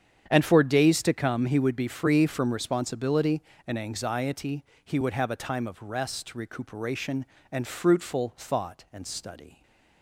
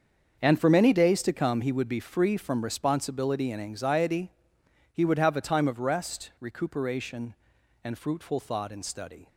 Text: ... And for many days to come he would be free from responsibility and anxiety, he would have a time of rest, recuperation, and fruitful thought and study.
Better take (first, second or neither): second